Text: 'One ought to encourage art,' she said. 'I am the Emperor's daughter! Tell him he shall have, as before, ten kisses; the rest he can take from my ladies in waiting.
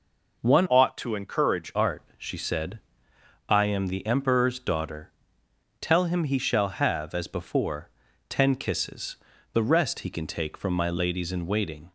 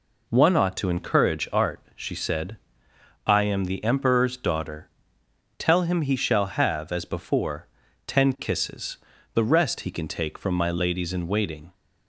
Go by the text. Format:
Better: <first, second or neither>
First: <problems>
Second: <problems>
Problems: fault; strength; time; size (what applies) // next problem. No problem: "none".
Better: second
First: changes voice from "ought" to "encourage"; from 0.6 to 1.7 s; 1.1 s long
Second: none